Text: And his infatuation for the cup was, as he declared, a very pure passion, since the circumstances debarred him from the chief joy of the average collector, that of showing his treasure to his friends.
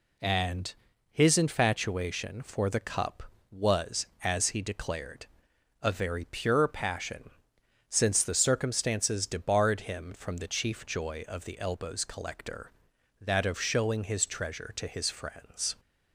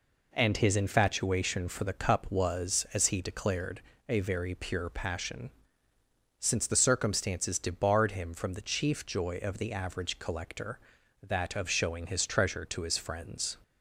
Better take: second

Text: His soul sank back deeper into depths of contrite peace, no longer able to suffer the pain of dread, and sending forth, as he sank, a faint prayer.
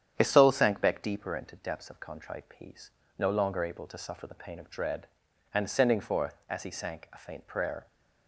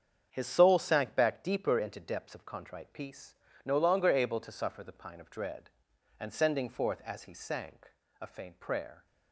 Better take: first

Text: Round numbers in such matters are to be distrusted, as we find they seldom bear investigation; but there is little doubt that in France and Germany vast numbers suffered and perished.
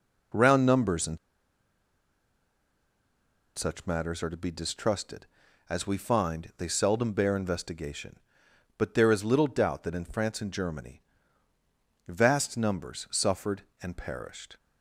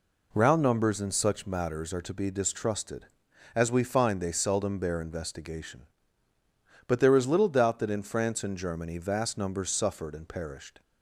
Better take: second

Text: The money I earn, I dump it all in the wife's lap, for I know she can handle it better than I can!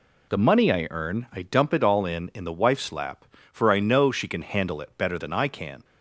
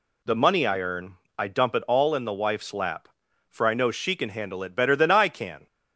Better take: second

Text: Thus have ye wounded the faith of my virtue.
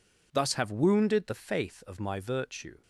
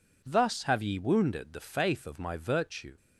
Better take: second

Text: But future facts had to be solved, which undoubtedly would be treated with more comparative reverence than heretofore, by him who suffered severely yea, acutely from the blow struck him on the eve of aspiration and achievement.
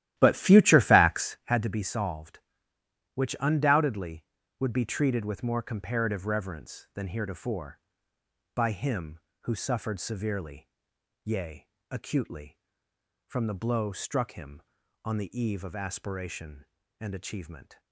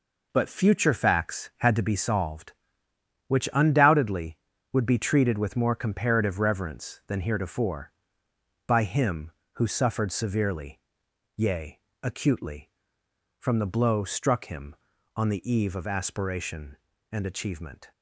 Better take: second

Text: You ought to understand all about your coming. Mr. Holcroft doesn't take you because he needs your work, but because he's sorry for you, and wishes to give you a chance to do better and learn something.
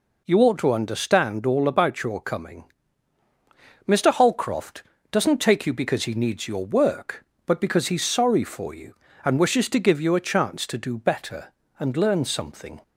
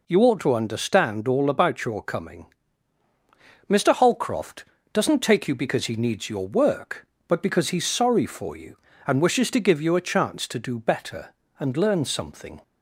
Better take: neither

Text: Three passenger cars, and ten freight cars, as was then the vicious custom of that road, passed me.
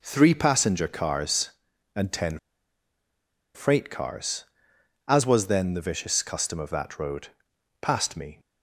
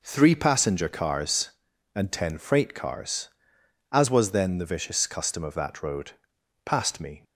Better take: second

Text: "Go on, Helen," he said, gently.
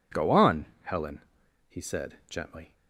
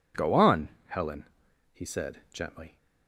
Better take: neither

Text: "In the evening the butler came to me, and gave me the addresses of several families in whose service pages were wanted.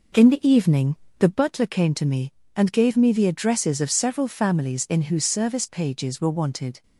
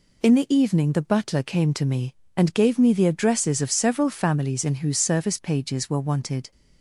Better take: second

